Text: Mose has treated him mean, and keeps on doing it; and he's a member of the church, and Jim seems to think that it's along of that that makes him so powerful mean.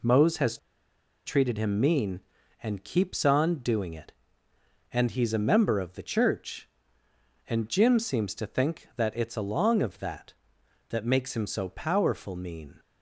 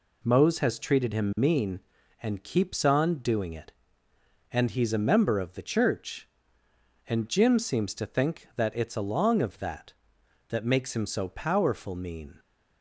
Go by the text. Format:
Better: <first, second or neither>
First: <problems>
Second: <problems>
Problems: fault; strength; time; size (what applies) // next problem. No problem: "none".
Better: second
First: pauses between "has" and "treated"; noticeable; at 0.5 s; 0.68 s long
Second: none